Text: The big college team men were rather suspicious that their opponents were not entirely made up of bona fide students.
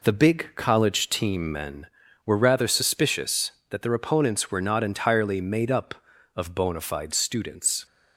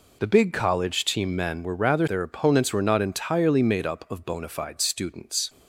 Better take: first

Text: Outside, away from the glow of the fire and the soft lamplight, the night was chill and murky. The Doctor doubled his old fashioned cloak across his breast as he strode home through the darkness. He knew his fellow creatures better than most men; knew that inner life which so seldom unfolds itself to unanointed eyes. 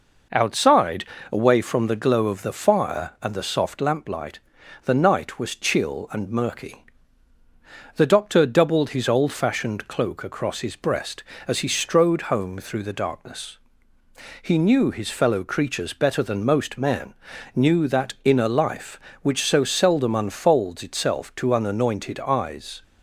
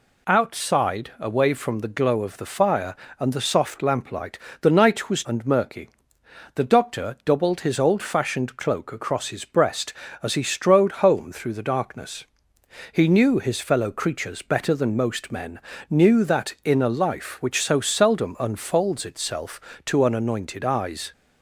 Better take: first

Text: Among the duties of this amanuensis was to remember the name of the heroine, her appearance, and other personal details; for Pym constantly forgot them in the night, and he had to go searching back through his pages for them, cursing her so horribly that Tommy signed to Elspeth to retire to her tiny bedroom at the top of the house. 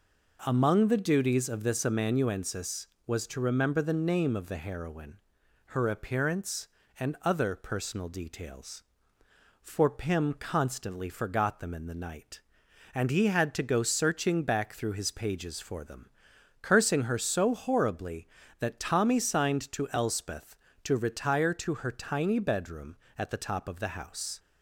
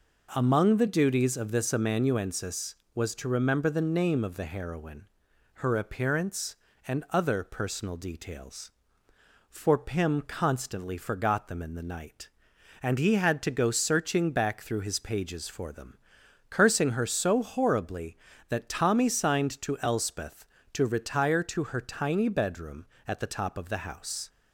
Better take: neither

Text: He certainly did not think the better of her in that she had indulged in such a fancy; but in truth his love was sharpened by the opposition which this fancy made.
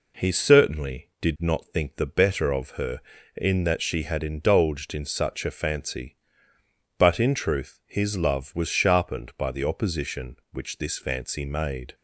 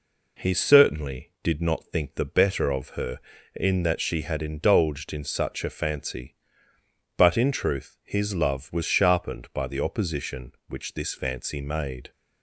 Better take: neither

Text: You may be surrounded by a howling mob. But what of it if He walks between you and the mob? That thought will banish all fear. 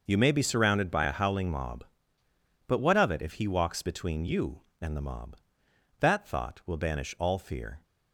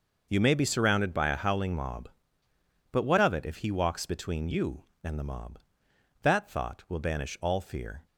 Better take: neither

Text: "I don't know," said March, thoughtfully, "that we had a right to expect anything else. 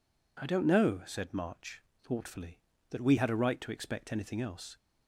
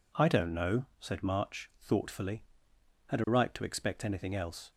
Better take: first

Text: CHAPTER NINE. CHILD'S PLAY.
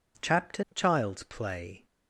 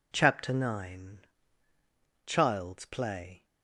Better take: second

